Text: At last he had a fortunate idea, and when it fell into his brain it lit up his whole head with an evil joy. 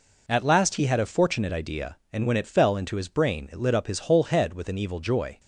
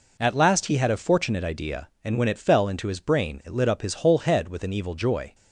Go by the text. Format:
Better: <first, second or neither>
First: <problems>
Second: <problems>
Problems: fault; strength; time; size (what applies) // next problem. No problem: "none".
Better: neither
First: none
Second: none